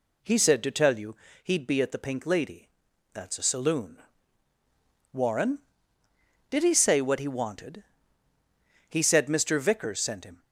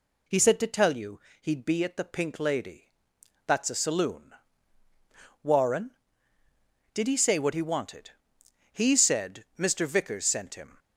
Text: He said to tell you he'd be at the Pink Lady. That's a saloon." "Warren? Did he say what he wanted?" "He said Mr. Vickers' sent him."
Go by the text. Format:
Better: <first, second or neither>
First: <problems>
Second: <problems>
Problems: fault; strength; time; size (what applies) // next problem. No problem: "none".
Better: neither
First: pauses between "you" and "he'd"; slight; at 1.1 s; 0.26 s long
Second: pauses between "you" and "he'd"; slight; at 1.2 s; 0.20 s long